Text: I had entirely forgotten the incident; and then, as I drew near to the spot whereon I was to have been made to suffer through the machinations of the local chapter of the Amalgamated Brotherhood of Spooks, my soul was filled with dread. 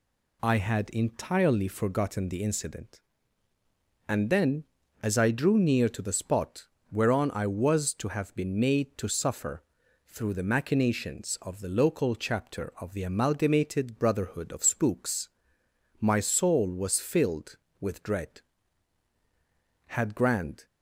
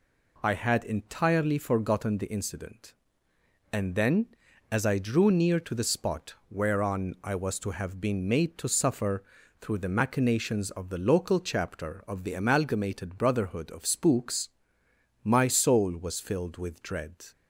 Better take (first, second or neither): second